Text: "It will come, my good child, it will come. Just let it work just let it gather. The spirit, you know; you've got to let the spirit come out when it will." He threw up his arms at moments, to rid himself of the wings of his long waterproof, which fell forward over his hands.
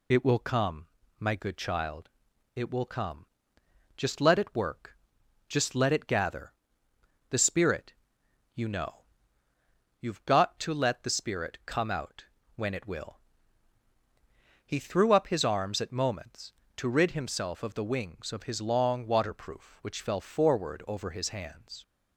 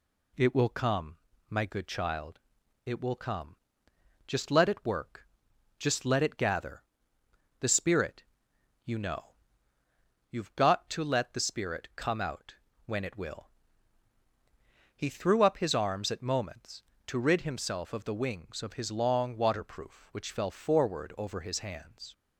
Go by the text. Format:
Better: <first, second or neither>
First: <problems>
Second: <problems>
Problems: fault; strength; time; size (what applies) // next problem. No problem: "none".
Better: second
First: loses the start of "It"; at 0.1 s; 45 ms // pauses between "work" and "just"; noticeable; at 4.9 s; 0.52 s long // pauses between "out" and "when"; slight; at 12.2 s; 0.32 s long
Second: pauses between "work" and "just"; noticeable; at 5.2 s; 0.52 s long // pauses between "out" and "when"; slight; at 12.5 s; 0.32 s long